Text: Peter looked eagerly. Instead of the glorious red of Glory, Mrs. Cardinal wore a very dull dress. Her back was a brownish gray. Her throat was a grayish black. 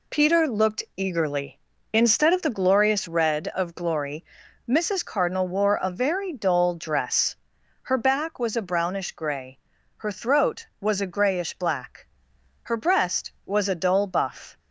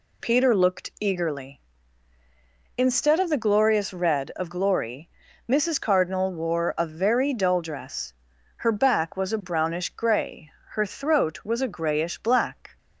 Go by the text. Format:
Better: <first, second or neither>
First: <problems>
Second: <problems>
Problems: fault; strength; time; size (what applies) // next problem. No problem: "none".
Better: second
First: goes on to say "Her breast was a dull buff"; strong; from 12.6 s on; 1.9 s long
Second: none